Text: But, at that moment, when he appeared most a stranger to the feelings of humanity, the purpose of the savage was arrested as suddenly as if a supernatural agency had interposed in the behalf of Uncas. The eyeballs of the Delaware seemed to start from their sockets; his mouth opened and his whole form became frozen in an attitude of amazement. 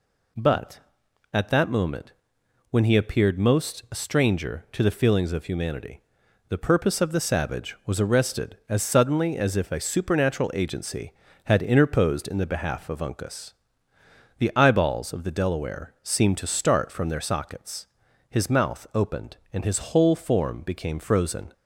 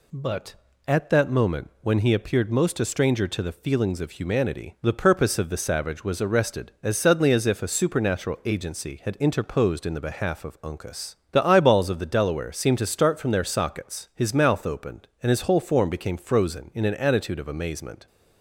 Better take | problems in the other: second | stops before "in an attitude of amazement"; at 21.5 s

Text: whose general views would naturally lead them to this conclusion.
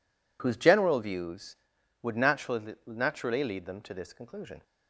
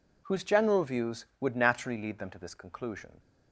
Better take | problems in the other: second | says "naturally" twice; at 2.8 s

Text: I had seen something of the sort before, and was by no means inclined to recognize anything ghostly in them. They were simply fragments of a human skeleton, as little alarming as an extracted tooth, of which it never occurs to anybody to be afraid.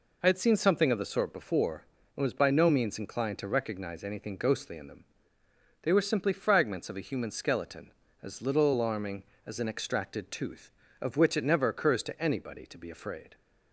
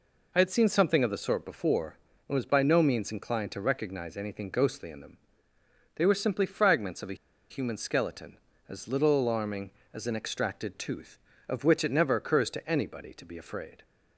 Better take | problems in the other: first | pauses between "a" and "human"; slight; at 7.1 s; 0.35 s long

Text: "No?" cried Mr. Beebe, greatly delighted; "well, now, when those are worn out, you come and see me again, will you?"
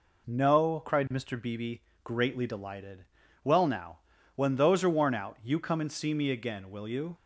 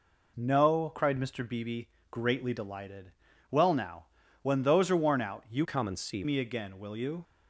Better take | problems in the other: first | changes voice from "come" to "see"; from 5.6 to 6.2 s; 0.6 s long

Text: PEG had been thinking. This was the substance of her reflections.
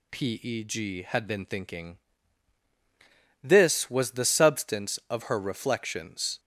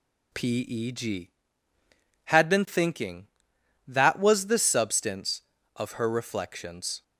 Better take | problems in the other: first | says "That" for "This"; at 3.8 s

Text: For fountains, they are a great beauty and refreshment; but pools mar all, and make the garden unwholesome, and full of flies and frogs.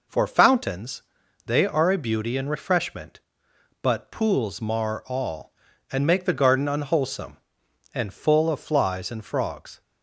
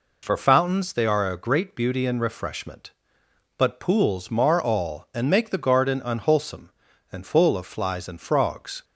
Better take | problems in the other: second | skips "great"; at 1.9 s

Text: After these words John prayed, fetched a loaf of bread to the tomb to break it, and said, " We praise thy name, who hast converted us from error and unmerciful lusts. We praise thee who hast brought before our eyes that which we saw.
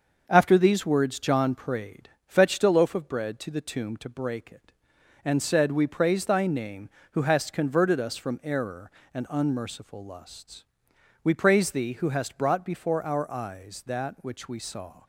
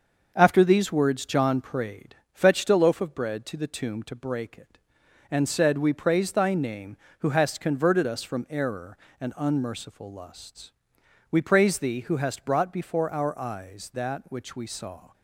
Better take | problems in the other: neither | starts louder than the rest; the same in both

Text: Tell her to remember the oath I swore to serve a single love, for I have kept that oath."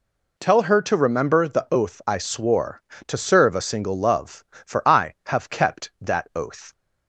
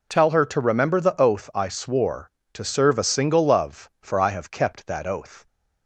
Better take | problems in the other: neither | none

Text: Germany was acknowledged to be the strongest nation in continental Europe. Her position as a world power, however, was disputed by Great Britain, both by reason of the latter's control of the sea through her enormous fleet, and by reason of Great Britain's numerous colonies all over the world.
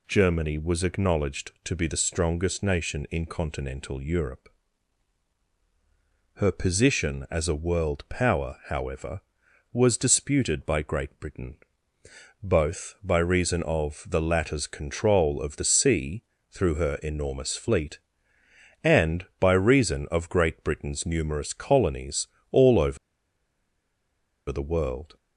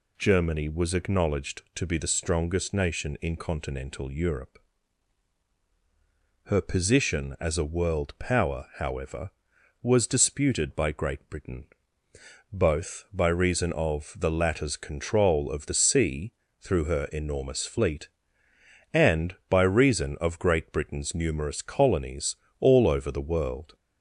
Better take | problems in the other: second | pauses between "sea" and "through"; slight; at 16.2 s; 0.28 s long; slight in the second // pauses between "colonies" and "all"; slight; at 22.2 s; 0.24 s long; slight in the second // pauses between "over" and "the"; strong; at 22.9 s; 1.5 s long

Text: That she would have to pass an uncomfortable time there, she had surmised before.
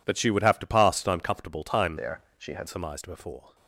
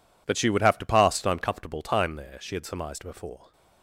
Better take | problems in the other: second | changes voice from "there" to "had"; from 1.9 to 2.6 s; 0.7 s long

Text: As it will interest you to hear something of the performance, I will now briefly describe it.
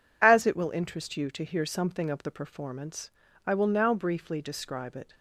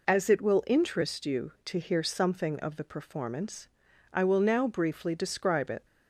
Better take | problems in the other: neither | none

